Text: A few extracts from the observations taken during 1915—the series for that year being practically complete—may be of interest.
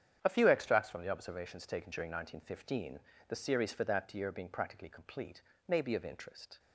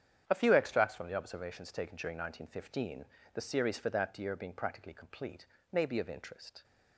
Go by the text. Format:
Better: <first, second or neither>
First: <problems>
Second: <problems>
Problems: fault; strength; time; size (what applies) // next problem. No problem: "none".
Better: neither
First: starts louder than the rest; strong; until 1.2 s; 8.5 dB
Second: starts louder than the rest; strong; until 1.2 s; 8.5 dB